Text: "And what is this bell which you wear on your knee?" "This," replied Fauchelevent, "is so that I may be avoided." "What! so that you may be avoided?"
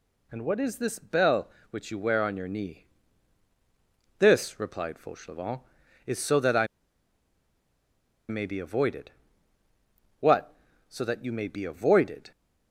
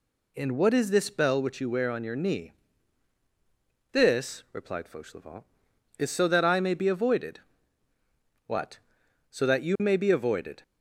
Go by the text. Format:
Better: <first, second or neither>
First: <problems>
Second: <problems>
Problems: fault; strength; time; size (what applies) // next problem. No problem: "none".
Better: second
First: pauses between "I" and "may"; strong; at 6.6 s; 1.6 s long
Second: none